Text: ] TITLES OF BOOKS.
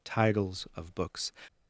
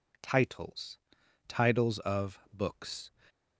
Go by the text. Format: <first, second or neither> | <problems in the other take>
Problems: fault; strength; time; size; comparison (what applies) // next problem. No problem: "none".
first | says "TITLES" twice; at 1.4 s